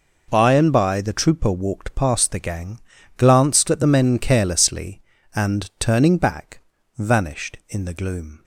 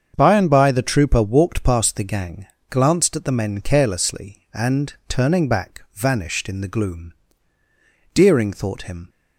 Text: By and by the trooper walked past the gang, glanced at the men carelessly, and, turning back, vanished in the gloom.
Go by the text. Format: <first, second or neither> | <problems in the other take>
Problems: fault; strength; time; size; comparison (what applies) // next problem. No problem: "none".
first | starts louder than the rest; until 1.1 s; 7 dB // goes on to say "Deering thought him"; noticeable; from 8.1 s on; 0.96 s long